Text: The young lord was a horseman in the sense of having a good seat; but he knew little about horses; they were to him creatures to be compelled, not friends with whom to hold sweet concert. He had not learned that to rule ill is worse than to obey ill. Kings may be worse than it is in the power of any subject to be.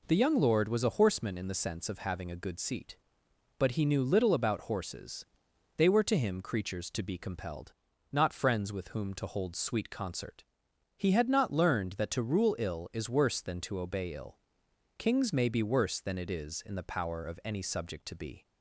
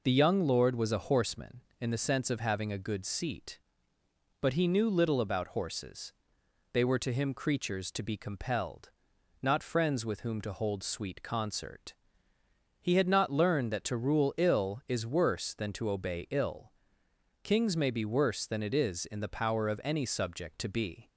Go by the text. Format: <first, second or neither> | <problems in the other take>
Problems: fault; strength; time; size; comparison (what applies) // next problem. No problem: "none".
neither | none